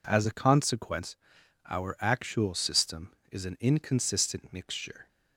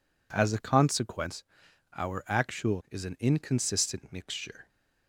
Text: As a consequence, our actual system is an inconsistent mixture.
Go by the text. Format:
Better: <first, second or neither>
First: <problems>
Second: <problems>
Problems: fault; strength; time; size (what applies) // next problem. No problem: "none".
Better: first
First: none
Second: skips "system"; at 2.8 s